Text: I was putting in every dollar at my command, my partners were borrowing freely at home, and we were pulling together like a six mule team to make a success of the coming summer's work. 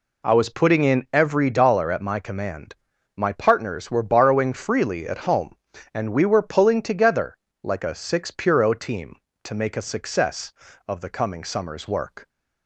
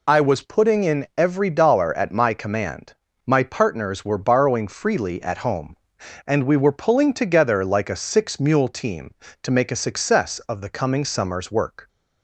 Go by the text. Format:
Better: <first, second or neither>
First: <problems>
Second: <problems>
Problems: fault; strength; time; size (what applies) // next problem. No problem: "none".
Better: second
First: pauses between "together" and "like"; slight; at 7.3 s; 0.30 s long // says "puro" for "mule"; at 8.3 s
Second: none